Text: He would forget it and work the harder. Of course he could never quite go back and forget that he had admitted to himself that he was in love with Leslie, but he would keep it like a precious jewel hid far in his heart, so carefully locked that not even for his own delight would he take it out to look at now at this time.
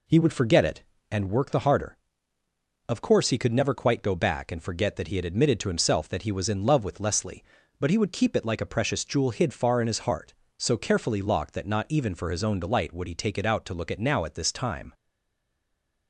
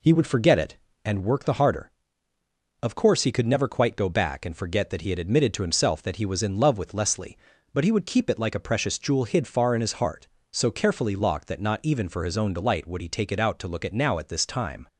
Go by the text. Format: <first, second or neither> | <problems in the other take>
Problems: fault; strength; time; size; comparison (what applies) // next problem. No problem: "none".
second | stays silent after the last word; noticeable; from 14.9 s on; 1.1 s long